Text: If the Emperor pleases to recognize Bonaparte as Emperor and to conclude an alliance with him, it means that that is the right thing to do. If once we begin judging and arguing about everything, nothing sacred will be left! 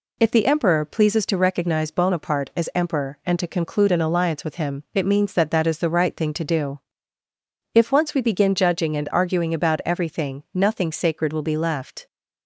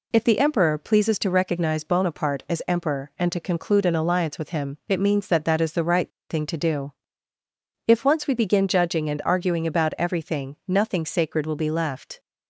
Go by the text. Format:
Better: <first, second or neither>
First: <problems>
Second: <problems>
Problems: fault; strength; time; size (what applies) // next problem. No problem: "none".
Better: first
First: none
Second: pauses between "right" and "thing"; slight; at 6.1 s; 0.19 s long